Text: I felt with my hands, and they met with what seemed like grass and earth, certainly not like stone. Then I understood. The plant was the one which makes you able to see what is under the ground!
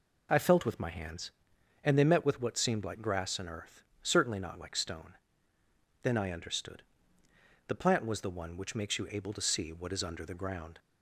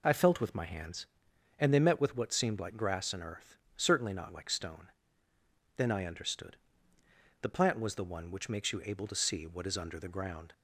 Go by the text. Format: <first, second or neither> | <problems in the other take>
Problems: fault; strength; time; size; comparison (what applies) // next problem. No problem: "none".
neither | none